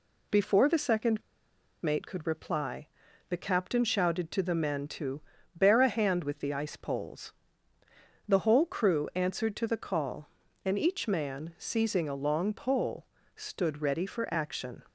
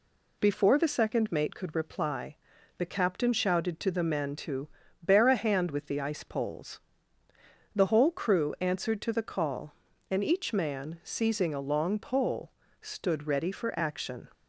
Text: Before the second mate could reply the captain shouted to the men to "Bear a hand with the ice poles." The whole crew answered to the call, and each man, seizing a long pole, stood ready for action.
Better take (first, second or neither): second